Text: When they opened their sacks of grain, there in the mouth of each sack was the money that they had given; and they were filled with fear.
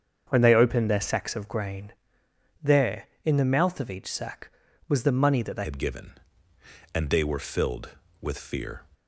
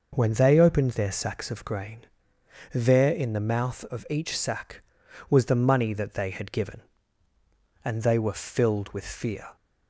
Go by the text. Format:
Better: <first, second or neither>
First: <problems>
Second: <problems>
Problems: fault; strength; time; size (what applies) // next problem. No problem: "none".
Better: second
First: starts louder than the rest; strong; until 1.2 s; 7 dB // changes voice at "had"; from 5.6 s on; 3.2 s long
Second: none